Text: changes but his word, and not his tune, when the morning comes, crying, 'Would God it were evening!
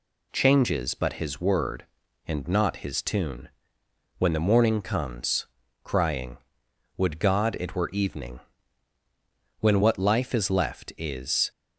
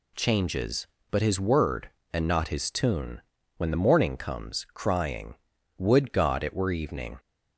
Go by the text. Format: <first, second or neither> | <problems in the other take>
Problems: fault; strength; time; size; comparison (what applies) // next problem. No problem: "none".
second | goes on to say "when what life is left is"; strong; from 9.6 s on; 1.8 s long